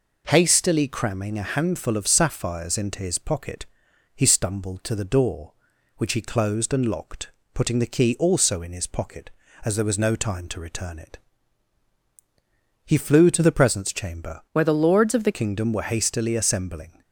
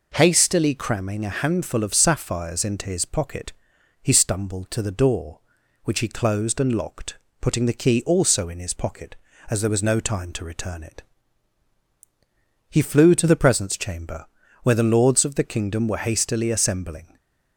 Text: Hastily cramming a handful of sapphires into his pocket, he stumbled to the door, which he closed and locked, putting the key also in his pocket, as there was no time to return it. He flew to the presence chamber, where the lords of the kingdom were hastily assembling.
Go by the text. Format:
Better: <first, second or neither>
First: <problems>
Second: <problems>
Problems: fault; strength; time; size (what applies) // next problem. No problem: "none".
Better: second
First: changes voice from "where" to "the"; from 14.5 to 15.3 s; 0.8 s long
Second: none